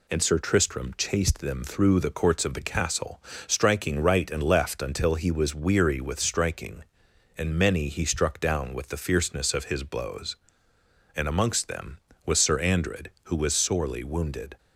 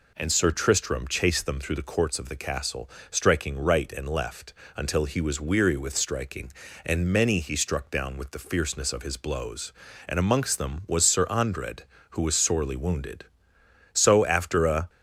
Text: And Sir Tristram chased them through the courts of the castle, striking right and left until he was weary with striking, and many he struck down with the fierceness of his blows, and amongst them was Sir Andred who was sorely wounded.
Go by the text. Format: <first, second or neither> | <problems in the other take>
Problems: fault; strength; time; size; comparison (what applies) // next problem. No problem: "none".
first | pauses between "left" and "until"; slight; at 4.5 s; 0.24 s long // goes on to say "So after a"; noticeable; from 13.9 s on; 0.96 s long